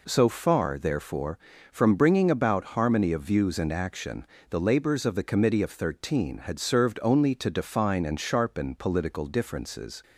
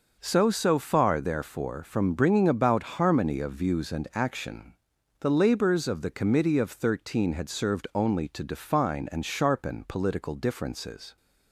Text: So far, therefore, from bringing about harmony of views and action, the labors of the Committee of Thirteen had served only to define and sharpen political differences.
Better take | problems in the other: first | starts louder than the rest; noticeable; until 1.2 s; 6 dB // says "So" twice; at 0.5 s

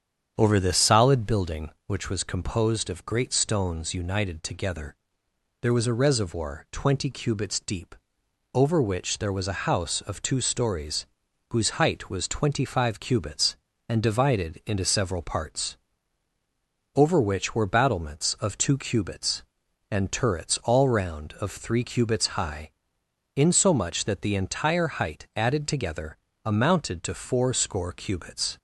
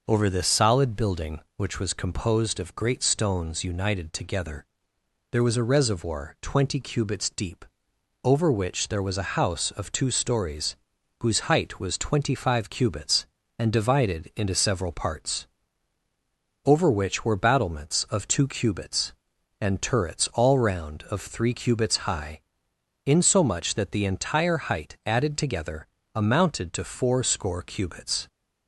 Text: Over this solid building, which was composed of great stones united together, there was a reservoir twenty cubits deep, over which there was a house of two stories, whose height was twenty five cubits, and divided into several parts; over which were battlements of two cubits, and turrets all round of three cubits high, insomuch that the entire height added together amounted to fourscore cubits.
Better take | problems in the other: second | starts louder than the rest; strong; until 1.5 s; 8 dB // pauses between "together" and "amounted"; slight; at 26.1 s; 0.30 s long; slight in the second

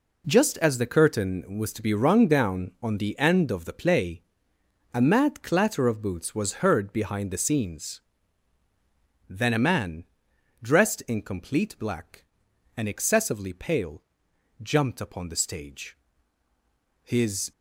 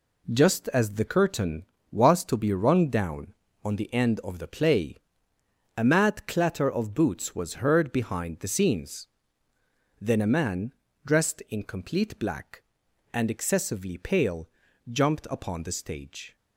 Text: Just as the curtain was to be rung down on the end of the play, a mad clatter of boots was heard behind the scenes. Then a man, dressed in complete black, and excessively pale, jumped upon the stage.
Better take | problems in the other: second | goes on to say "His"; slight; from 17.0 s on; 0.48 s long

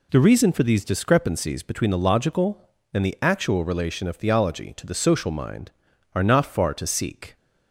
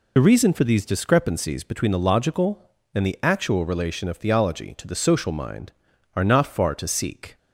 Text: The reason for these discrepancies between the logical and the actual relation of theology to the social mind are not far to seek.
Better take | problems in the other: first | loses the start of "The"; at 0.1 s; 50 ms

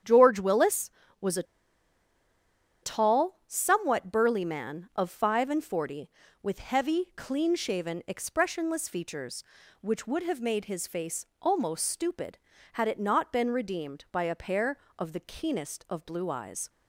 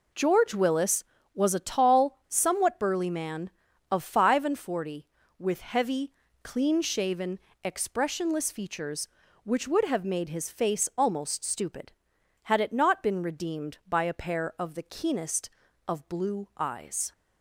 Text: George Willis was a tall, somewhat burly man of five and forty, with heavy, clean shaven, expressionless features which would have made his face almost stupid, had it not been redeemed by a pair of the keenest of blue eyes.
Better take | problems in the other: second | starts louder than the rest; strong; until 1.3 s; 8.5 dB // pauses between "a" and "tall"; strong; at 1.4 s; 1.3 s long // pauses between "face" and "almost"; slight; at 11.2 s; 0.16 s long

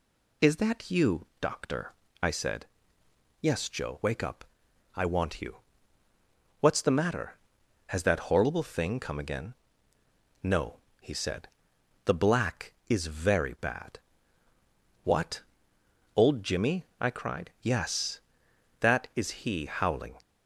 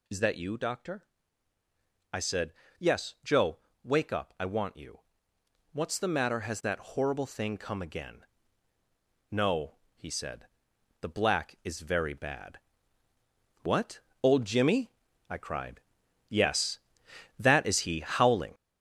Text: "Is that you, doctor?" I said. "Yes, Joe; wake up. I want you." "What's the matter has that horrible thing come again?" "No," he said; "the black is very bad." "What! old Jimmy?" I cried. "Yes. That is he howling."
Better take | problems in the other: first | gets louder; strong; throughout; 7.5 dB

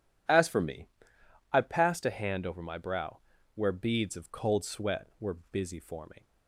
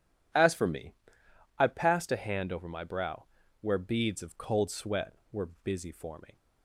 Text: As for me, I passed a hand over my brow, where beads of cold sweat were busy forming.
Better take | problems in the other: neither | pauses between "were" and "busy"; slight; the same in both

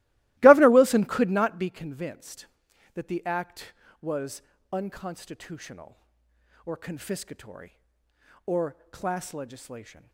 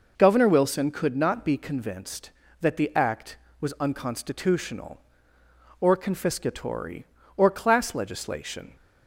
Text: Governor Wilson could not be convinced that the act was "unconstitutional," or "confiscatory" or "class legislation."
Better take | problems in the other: second | starts louder than the rest; strong; until 1.8 s; 18 dB // pauses between "was" and "unconstitutional"; slight; at 4.4 s; 0.30 s long // pauses between "or" and "class"; slight; at 8.7 s; 0.16 s long

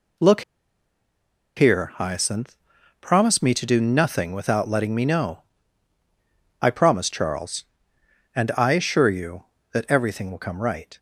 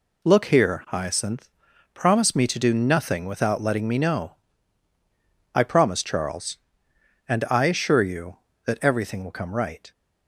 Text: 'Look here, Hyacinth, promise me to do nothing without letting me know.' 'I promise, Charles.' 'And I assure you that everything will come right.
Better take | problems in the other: second | pauses between "Look" and "here"; at 0.4 s; 1.1 s long

